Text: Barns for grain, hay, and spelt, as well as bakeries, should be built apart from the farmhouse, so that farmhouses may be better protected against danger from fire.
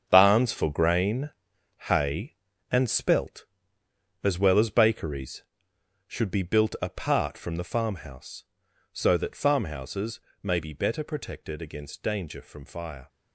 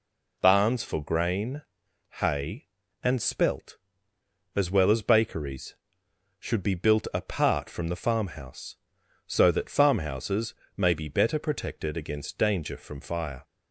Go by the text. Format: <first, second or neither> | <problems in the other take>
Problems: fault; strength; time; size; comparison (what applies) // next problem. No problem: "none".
second | gets quieter; strong; throughout; 10.5 dB // pauses between "farmhouses" and "may"; slight; at 10.1 s; 0.24 s long; slight in the second